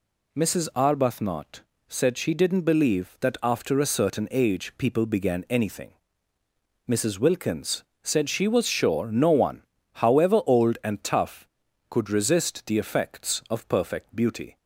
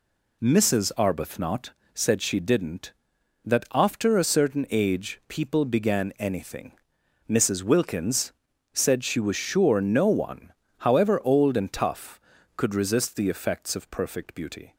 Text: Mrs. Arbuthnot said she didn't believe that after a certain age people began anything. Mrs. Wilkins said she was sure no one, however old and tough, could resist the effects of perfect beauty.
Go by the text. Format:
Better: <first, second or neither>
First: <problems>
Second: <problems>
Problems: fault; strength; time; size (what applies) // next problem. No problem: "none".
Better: first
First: pauses between "Arbuthnot" and "said"; slight; at 1.6 s; 0.26 s long // pauses between "Wilkins" and "said"; slight; at 7.8 s; 0.22 s long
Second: pauses between "Arbuthnot" and "said"; slight; at 1.7 s; 0.22 s long // skips "believe"; at 3.1 s // pauses between "Wilkins" and "said"; at 8.3 s; 0.42 s long